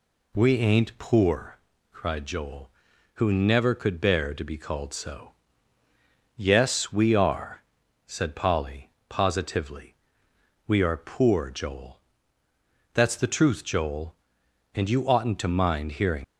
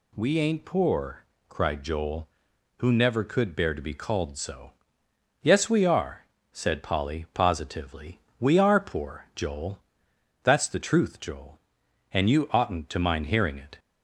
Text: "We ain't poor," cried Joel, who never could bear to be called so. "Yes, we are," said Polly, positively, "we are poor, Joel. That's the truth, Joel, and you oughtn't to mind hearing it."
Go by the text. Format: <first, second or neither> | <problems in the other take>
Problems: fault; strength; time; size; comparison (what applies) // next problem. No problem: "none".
second | stops before "it"; at 16.2 s